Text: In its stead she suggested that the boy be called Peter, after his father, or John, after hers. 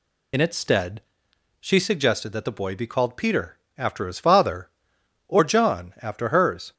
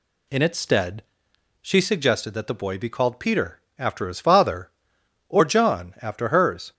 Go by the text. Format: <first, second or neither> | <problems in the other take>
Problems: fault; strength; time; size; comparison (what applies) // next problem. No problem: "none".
second | loses the start of "In"; at 0.3 s; 55 ms // pauses between "stead" and "she"; noticeable; at 1.0 s; 0.58 s long; noticeable in the second